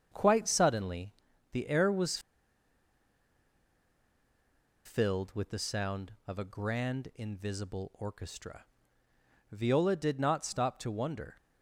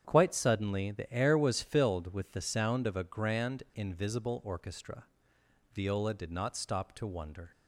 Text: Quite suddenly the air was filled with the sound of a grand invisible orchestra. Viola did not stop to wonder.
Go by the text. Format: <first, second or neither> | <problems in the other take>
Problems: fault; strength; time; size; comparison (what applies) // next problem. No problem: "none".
second | starts louder than the rest; strong; until 1.1 s; 7 dB; strong in the second // pauses between "suddenly" and "the"; at 1.1 s; 0.38 s long // pauses between "was" and "filled"; strong; at 2.1 s; 2.6 s long